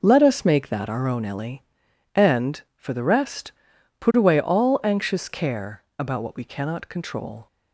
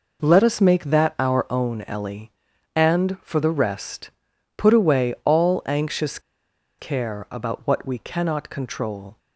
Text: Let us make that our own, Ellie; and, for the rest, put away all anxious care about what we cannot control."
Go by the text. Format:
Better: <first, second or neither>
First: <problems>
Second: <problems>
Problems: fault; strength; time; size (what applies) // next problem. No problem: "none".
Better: first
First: none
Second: pauses between "anxious" and "care"; noticeable; at 6.1 s; 0.60 s long